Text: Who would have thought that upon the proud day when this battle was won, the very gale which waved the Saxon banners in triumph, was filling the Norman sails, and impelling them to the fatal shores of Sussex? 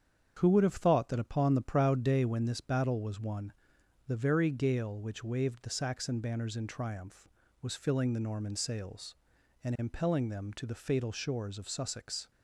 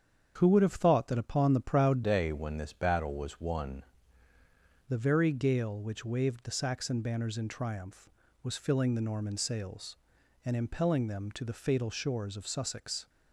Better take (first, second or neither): first